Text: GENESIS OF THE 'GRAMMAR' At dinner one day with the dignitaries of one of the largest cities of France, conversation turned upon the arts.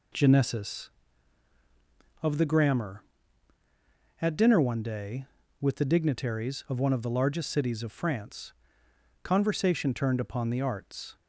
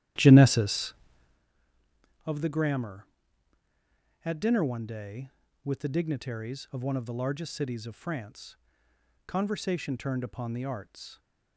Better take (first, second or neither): first